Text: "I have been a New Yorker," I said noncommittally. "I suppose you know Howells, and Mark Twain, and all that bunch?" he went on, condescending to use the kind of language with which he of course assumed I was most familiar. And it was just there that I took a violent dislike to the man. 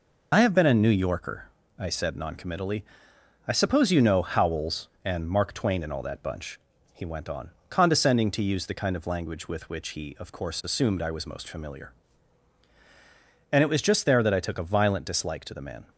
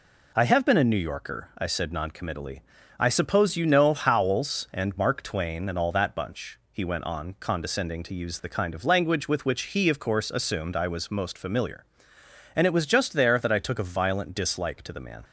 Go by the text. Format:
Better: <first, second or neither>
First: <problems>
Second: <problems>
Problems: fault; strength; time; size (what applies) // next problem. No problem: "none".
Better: second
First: loses the start of "I"; at 0.3 s; 35 ms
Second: none